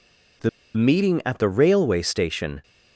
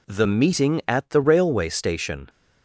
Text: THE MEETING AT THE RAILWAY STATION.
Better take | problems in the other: second | pauses between "THE" and "MEETING"; slight; at 0.4 s; 0.27 s long

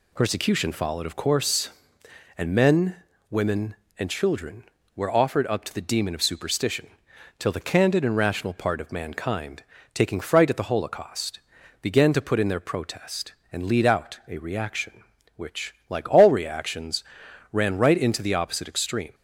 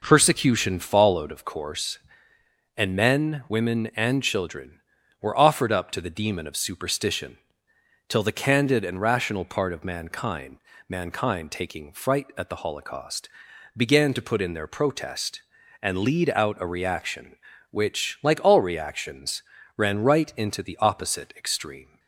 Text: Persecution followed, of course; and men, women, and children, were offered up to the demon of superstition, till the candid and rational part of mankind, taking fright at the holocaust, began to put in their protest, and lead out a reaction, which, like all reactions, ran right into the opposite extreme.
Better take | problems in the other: first | says "mankind" twice; at 10.8 s

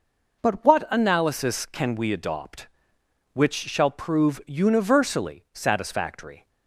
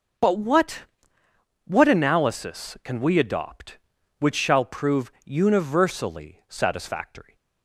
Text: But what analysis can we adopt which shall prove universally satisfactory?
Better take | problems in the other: first | says "what" twice; at 1.6 s

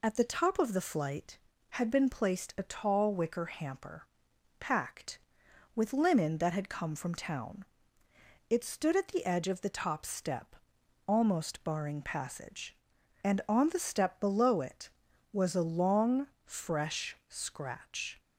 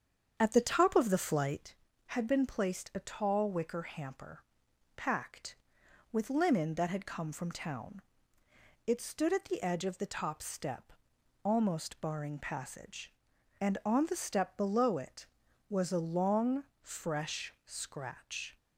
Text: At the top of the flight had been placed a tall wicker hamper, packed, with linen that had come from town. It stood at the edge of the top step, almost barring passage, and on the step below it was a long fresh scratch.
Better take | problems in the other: first | starts louder than the rest; strong; until 1.7 s; 7.5 dB // pauses between "long" and "fresh"; slight; at 16.6 s; 0.18 s long; slight in the first

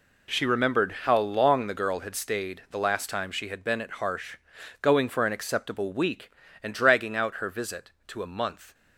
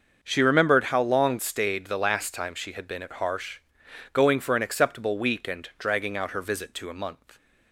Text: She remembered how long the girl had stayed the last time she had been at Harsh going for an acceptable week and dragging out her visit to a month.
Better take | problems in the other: first | starts louder than the rest; until 1.2 s; 6 dB // skips "the girl had"; at 1.3 s // pauses between "Harsh" and "going"; noticeable; at 3.5 s; 0.54 s long; also in the first

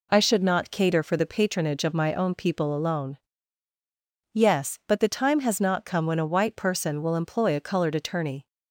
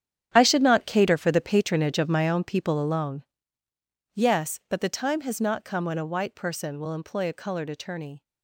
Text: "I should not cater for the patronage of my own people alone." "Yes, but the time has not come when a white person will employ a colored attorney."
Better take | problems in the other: first | gets quieter; strong; throughout; 13.5 dB

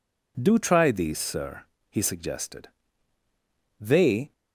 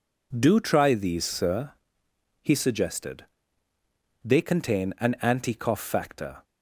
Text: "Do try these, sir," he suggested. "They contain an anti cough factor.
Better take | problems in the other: second | stops before "contain an anti cough factor"; at 4.3 s

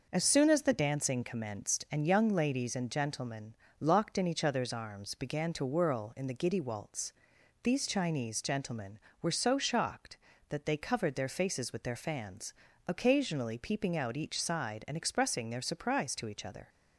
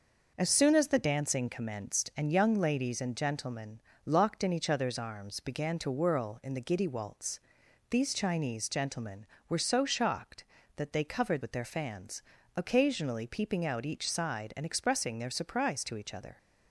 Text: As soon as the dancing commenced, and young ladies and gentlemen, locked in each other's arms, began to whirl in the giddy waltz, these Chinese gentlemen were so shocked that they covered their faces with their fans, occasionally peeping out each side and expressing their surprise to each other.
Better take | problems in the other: first | skips "their faces"; at 11.4 s

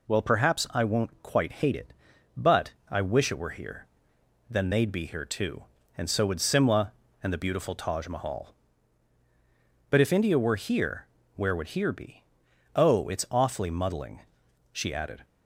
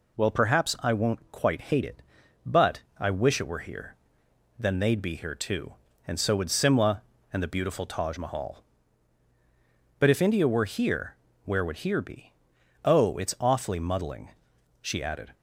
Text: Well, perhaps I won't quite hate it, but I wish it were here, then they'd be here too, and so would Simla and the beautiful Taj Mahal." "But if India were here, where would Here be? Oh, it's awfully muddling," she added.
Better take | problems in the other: neither | pauses between "but" and "I"; slight; the same in both

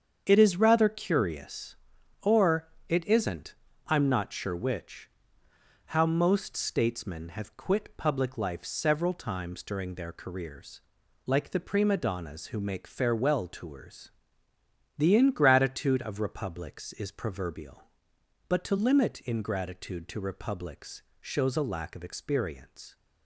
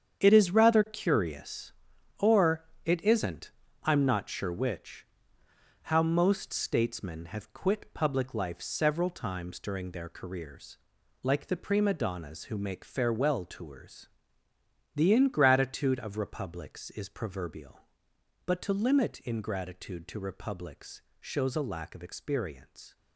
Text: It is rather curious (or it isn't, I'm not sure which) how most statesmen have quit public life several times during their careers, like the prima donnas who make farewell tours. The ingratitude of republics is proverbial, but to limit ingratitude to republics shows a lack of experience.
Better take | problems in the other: first | gets quieter; strong; throughout; 10 dB // starts louder than the rest; strong; until 1.2 s; 8 dB; strong in the first // pauses between "or" and "it"; slight; at 2.6 s; 0.20 s long; slight in the first // pauses between "republics" and "shows"; slight; at 21.0 s; 0.16 s long; slight in the first

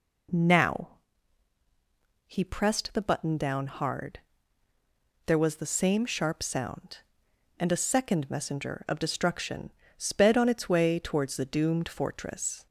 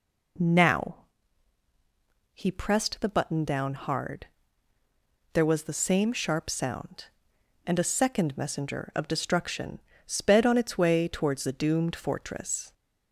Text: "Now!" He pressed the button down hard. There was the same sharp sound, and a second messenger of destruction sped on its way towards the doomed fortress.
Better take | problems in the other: neither | pauses between "destruction" and "sped"; slight; the same in both

